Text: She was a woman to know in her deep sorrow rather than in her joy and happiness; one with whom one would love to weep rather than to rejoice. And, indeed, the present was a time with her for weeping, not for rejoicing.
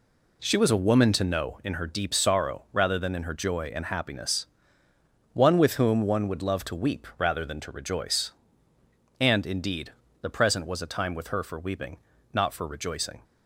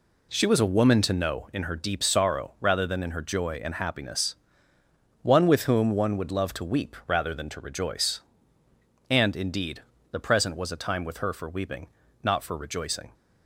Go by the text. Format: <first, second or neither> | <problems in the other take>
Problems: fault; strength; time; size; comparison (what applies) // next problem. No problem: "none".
neither | none